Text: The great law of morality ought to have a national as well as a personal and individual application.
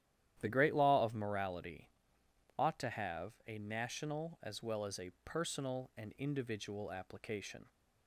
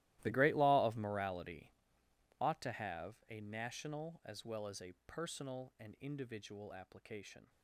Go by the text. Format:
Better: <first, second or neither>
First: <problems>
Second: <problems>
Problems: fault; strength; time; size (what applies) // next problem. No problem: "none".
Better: first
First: starts louder than the rest; strong; until 1.4 s; 11.5 dB // pauses between "morality" and "ought"; noticeable; at 1.8 s; 0.70 s long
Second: gets quieter; strong; throughout; 18.5 dB // starts louder than the rest; strong; until 1.2 s; 16 dB // pauses between "morality" and "ought"; noticeable; at 1.7 s; 0.70 s long